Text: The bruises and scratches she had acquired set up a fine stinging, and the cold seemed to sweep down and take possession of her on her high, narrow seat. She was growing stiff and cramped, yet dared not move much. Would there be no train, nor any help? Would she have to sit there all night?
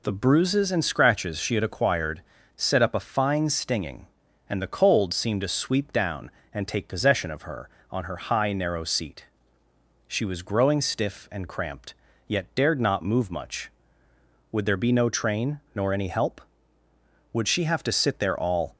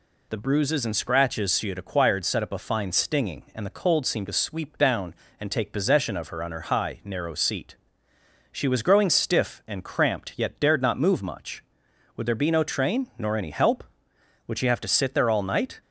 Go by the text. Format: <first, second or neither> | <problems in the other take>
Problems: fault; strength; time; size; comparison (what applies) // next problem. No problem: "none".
second | pauses between "acquired" and "set"; slight; at 2.2 s; 0.36 s long // stops before "night"; at 18.7 s